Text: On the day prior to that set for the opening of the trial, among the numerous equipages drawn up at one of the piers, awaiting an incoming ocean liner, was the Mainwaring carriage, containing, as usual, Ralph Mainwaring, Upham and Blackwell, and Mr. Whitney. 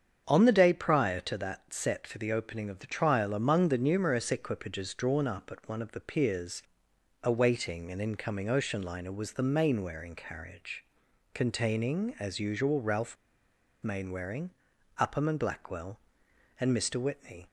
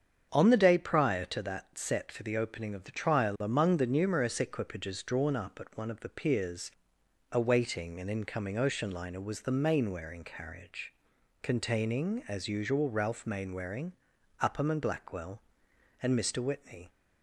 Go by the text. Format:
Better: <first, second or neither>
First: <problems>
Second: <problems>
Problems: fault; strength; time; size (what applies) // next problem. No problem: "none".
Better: second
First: starts louder than the rest; strong; until 1.2 s; 7.5 dB // pauses between "Ralph" and "Mainwaring"; noticeable; at 13.1 s; 0.69 s long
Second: starts louder than the rest; strong; until 1.3 s; 7.5 dB